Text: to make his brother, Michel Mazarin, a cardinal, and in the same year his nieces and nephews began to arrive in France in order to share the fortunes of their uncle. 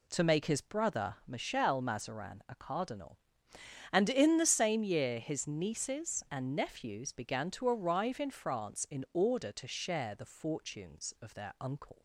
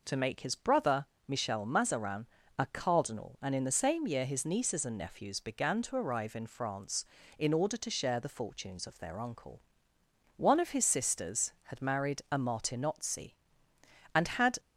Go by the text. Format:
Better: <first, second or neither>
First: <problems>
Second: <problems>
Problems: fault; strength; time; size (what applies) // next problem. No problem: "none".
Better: first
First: none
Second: goes on to say "One of his sisters had married a Martinozzi and had"; strong; from 10.3 s on; 4.2 s long